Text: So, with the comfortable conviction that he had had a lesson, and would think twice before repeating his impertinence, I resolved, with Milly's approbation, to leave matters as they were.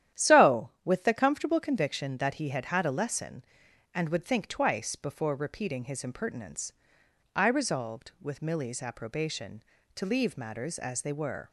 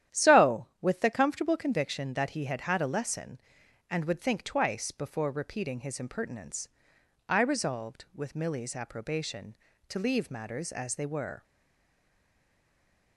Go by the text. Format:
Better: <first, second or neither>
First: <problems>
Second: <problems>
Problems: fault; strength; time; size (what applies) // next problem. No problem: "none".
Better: first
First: starts louder than the rest; strong; until 1.3 s; 11 dB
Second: starts louder than the rest; strong; until 1.2 s; 11 dB // stays silent after the last word; noticeable; from 11.4 s on; 1.7 s long